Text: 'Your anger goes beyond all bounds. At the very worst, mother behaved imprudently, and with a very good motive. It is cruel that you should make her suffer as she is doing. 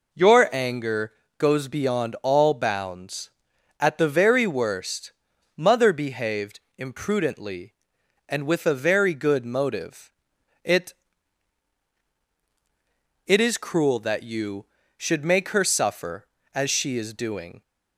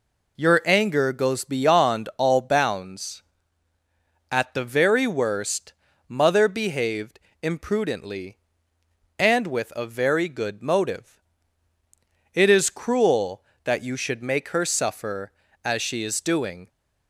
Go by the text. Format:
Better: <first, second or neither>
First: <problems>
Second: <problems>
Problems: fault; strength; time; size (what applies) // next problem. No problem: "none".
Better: second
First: pauses between "anger" and "goes"; slight; at 1.1 s; 0.24 s long // pauses between "behaved" and "imprudently"; slight; at 6.5 s; 0.18 s long // says "It" twice; at 13.2 s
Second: pauses between "behaved" and "imprudently"; slight; at 7.1 s; 0.24 s long